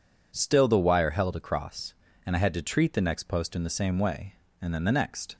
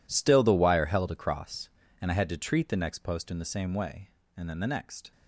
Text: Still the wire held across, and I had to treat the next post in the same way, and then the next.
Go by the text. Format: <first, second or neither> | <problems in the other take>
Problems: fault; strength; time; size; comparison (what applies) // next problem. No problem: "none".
first | gets quieter; strong; throughout; 17 dB